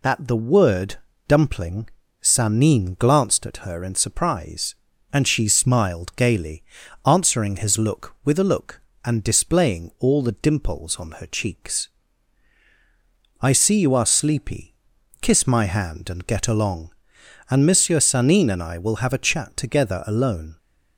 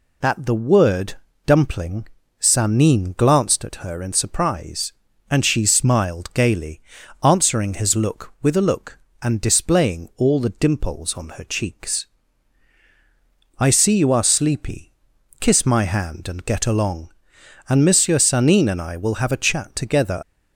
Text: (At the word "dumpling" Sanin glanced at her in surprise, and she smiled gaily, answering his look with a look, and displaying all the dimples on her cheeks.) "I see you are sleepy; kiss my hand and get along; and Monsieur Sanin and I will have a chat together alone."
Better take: first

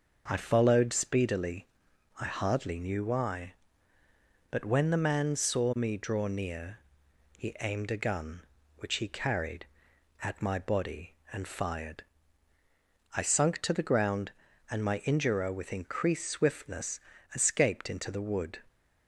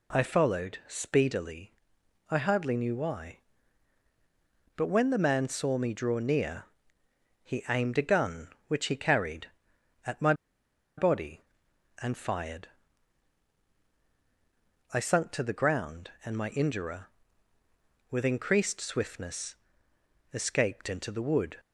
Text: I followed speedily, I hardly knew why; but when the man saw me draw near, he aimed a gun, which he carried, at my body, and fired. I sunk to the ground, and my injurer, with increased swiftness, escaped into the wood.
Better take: first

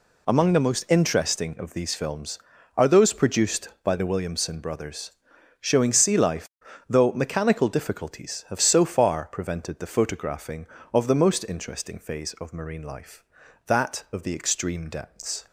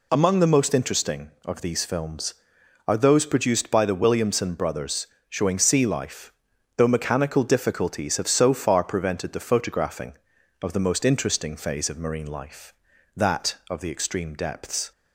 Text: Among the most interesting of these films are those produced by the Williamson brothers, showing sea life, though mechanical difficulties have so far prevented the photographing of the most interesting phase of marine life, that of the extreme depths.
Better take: neither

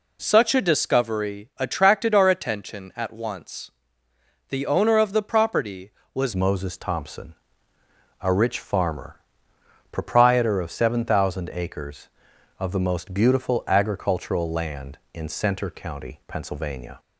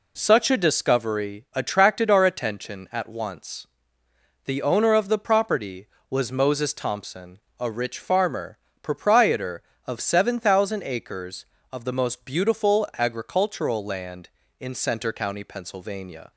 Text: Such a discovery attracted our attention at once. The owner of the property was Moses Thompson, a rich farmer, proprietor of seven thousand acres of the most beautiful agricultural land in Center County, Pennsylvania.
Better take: second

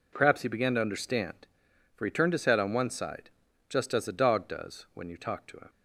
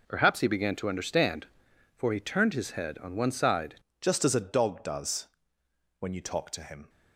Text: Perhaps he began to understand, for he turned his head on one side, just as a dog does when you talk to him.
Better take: first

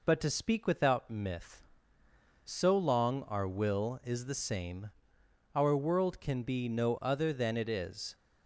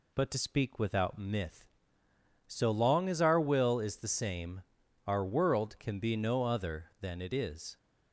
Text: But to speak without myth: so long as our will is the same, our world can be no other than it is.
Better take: second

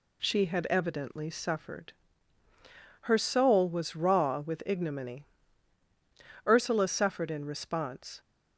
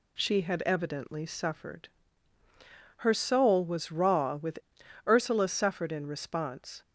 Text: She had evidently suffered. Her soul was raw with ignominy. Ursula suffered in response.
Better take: first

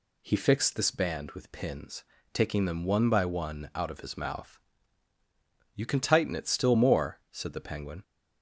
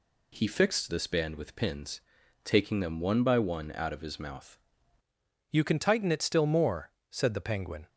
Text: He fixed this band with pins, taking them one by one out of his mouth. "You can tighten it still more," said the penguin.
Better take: first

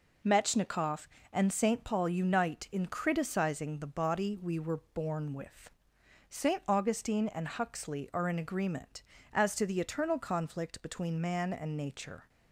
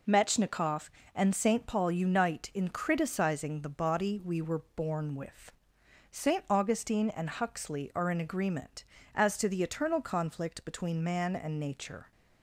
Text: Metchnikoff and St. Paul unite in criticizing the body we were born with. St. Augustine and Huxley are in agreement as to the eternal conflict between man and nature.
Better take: neither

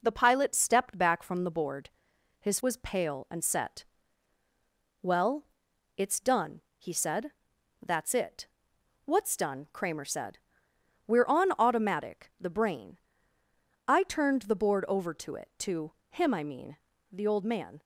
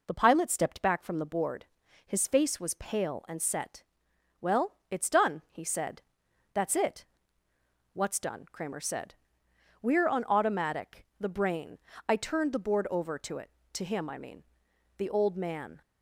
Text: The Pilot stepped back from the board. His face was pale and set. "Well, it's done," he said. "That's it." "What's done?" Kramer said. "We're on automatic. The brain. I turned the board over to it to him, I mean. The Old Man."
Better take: second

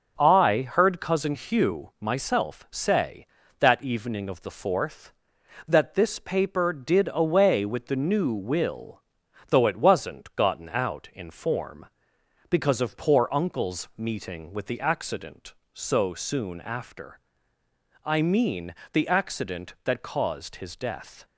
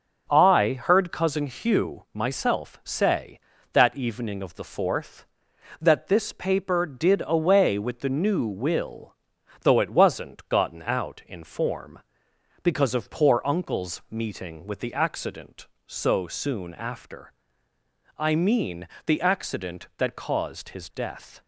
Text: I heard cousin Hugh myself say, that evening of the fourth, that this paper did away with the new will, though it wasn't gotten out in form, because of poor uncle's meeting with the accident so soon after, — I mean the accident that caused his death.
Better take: neither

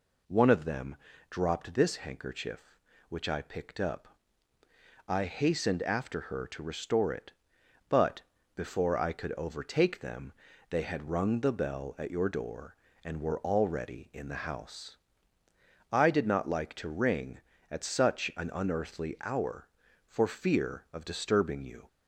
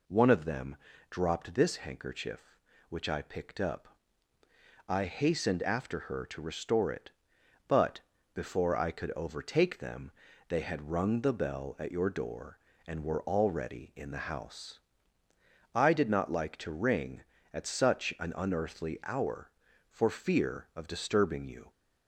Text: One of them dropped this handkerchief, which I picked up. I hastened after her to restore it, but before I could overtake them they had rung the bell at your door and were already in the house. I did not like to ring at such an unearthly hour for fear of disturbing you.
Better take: neither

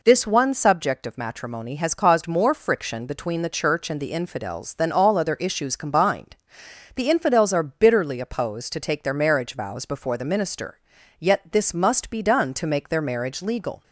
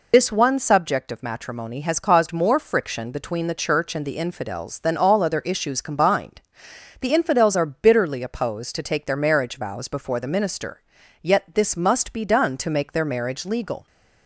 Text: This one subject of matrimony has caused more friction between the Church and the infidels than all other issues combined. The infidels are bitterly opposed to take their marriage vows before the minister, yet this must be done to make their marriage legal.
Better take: first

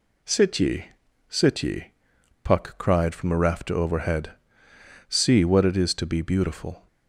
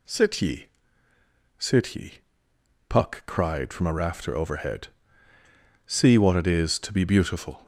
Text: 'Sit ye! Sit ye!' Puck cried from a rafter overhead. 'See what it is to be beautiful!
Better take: second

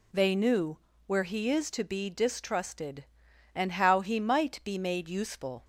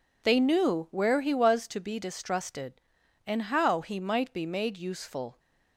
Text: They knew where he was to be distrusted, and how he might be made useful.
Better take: second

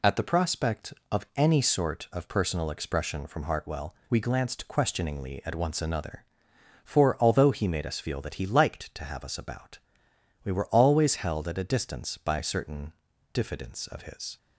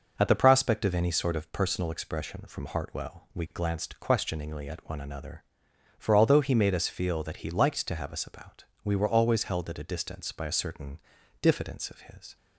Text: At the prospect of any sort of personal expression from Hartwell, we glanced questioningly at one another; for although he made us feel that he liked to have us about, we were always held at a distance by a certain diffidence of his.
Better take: second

